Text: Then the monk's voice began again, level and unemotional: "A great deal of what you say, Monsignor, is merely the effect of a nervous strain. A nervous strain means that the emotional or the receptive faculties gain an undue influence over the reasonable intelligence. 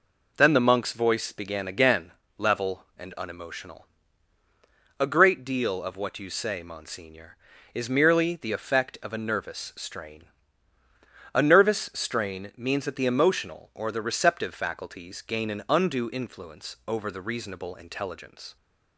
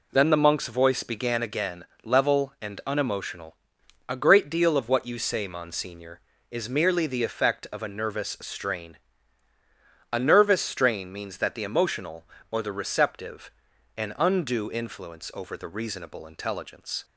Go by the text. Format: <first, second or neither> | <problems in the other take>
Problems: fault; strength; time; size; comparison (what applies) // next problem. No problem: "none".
first | skips "faculties gain"; at 13.7 s